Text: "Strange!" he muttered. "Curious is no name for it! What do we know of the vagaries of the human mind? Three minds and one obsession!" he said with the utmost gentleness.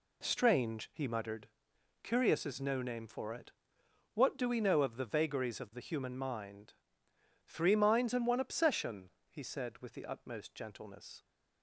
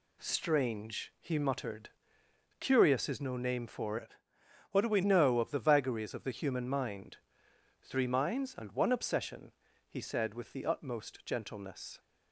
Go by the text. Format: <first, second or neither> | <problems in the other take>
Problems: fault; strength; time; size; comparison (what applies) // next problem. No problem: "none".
first | changes voice from "it" to "we"; from 3.9 to 5.0 s; 1.1 s long